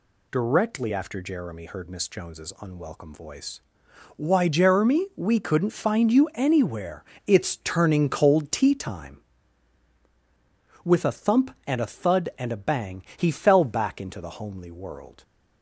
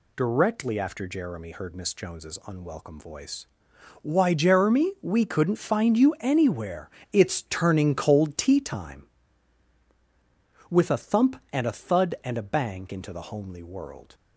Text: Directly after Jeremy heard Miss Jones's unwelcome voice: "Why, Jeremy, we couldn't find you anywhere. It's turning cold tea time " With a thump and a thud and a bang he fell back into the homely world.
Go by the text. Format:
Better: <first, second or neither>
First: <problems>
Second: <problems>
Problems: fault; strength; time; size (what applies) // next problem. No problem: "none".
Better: first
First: none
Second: skips "he fell back"; at 12.9 s